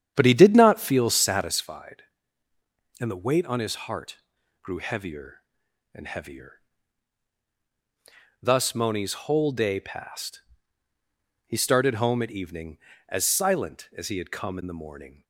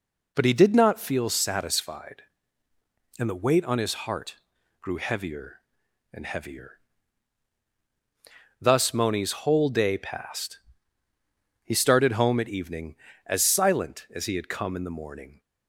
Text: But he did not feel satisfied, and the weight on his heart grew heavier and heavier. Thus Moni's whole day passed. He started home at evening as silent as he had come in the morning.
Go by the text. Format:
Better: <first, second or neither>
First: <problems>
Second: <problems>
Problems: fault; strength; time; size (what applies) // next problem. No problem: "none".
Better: second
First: starts louder than the rest; strong; until 1.6 s; 9 dB // pauses between "heart" and "grew"; at 4.1 s; 0.44 s long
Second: pauses between "heart" and "grew"; at 4.3 s; 0.44 s long